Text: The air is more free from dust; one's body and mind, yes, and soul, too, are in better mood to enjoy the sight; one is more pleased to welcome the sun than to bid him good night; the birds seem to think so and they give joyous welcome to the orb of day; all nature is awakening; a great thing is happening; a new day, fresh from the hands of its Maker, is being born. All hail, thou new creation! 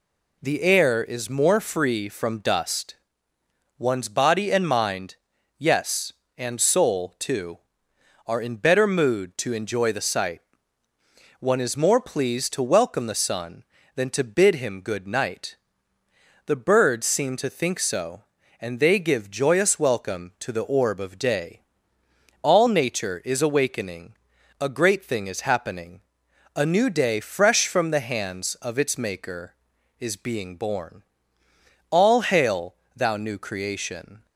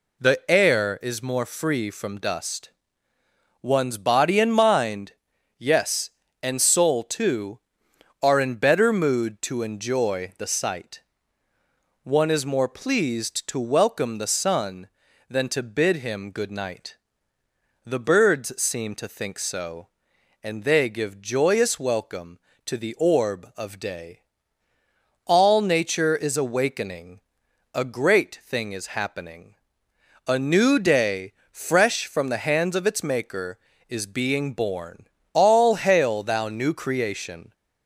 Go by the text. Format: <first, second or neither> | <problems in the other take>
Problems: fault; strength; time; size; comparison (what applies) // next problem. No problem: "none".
neither | none